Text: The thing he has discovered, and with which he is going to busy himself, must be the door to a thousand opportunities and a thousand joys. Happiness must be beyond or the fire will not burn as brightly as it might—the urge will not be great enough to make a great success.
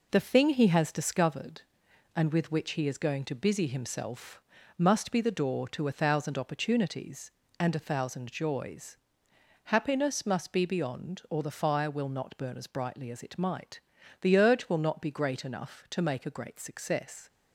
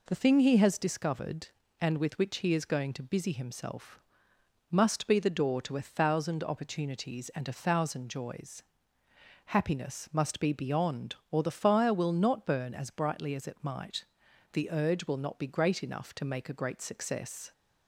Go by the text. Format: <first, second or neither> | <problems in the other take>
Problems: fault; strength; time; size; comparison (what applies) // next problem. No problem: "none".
second | gets quieter; noticeable; throughout; 5 dB